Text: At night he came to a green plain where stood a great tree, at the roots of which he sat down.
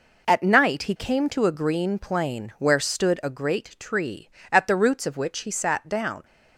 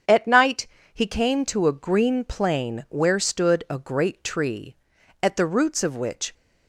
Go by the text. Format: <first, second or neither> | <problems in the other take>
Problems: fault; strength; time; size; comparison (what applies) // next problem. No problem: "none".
first | starts louder than the rest; strong; until 1.3 s; 7 dB // pauses between "night" and "he"; slight; at 0.6 s; 0.26 s long // stops before "he sat down"; at 6.3 s